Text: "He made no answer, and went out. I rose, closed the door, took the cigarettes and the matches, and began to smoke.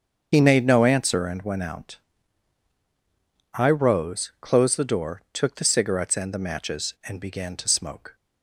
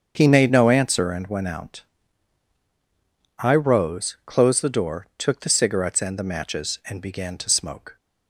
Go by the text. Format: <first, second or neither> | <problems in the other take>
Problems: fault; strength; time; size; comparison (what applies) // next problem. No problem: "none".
second | loses the start of "He"; at 0.3 s; 40 ms // starts louder than the rest; until 1.3 s; 7 dB; also in the second